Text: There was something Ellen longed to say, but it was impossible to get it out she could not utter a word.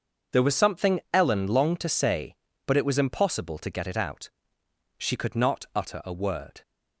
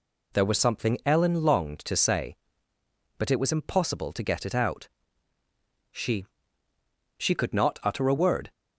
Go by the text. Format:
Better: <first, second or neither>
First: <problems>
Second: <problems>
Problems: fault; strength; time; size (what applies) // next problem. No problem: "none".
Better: first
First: pauses between "out" and "she"; noticeable; at 4.2 s; 0.68 s long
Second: pauses between "out" and "she"; at 4.8 s; 1.0 s long // says "she" twice; at 7.1 s